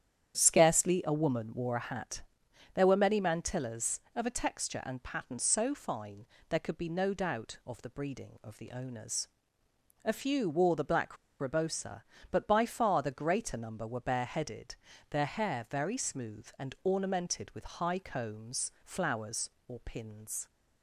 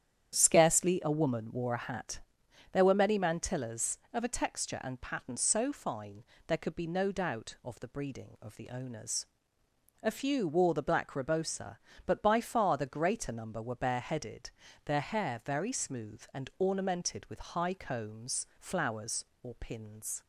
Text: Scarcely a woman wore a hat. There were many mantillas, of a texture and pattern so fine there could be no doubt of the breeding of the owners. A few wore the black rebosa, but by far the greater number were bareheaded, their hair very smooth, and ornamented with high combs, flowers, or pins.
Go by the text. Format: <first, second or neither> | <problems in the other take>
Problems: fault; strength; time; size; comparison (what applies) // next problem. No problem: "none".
second | starts louder than the rest; strong; until 1.4 s; 9.5 dB; strong in the second // pauses between "fine" and "there"; slight; at 6.2 s; 0.24 s long; slight in the second // pauses between "black" and "rebosa"; slight; at 11.1 s; 0.24 s long